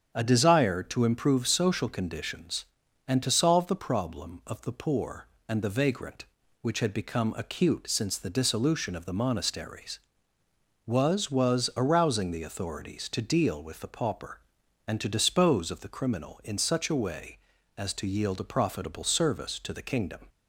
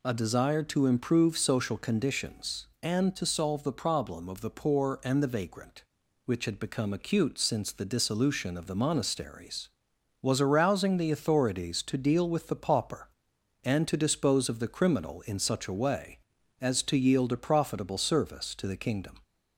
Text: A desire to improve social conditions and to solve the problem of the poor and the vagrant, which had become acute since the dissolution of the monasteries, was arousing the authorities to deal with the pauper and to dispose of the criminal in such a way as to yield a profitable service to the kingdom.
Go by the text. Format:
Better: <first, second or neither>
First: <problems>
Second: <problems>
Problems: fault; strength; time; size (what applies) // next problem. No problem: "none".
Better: second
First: starts louder than the rest; strong; until 1.1 s; 7.5 dB // says "was" twice; at 11.3 s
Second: none